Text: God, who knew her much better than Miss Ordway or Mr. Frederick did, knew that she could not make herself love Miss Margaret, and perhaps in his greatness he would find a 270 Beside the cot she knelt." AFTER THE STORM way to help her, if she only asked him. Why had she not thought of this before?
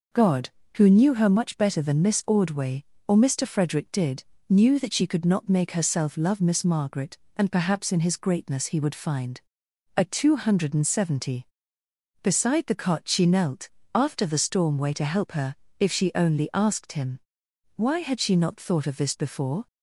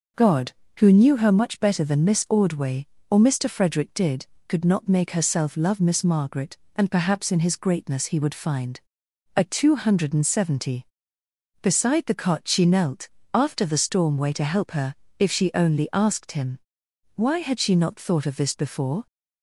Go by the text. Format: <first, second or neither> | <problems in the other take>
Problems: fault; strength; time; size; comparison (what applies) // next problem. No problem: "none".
first | skips "knew that she"; at 4.3 s // pauses between "find" and "a"; noticeable; at 8.8 s; 0.56 s long; noticeable in the first